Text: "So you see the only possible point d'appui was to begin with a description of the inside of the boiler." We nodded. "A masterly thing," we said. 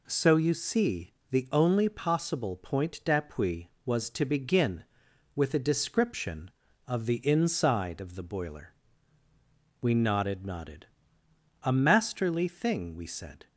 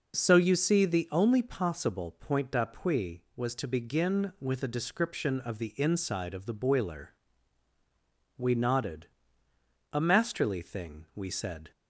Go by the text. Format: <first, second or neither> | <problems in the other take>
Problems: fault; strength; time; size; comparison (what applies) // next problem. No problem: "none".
second | pauses between "see" and "the"; slight; at 1.1 s; 0.18 s long // says "nodded" twice; at 10.4 s